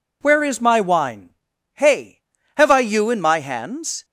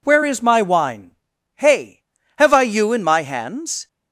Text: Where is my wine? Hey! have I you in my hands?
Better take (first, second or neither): neither